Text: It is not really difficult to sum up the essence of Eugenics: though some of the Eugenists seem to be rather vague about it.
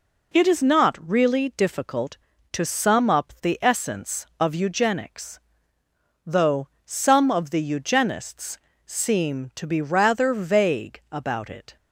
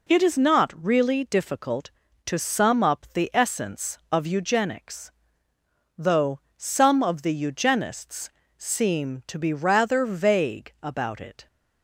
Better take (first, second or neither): neither